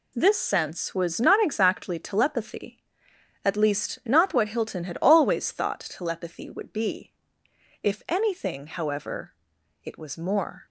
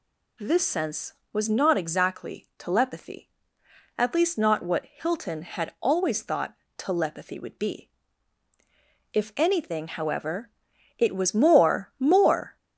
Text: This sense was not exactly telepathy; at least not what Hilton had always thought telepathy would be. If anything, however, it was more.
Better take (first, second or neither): first